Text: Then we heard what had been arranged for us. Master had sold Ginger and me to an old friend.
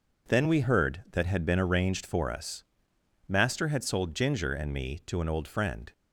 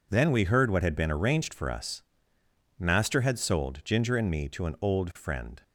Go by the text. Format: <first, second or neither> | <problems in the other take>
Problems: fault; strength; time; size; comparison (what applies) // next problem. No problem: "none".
second | says "that" for "what"; at 1.1 s